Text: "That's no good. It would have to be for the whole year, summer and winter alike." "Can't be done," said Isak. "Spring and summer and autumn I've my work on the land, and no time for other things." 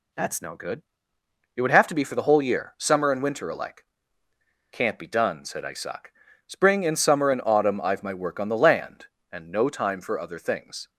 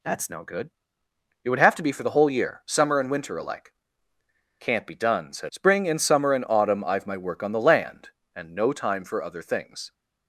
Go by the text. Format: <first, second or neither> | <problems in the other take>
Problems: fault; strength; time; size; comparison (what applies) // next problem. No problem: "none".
first | skips "Isak"; at 5.4 s